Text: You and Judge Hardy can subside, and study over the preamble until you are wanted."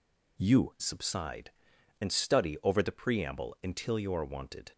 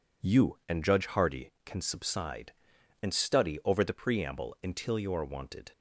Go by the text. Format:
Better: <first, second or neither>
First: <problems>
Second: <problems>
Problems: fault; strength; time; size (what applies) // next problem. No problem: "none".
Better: second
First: skips "and Judge Hardy can"; at 0.7 s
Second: none